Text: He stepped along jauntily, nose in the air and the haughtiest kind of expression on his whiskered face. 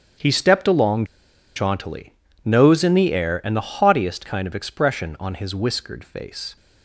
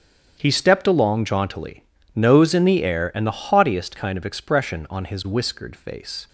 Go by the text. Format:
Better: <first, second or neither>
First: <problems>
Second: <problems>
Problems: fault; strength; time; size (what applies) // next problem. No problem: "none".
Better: second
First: starts louder than the rest; strong; until 1.7 s; 8.5 dB // pauses between "along" and "jauntily"; noticeable; at 1.0 s; 0.51 s long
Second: starts louder than the rest; strong; until 1.3 s; 8.5 dB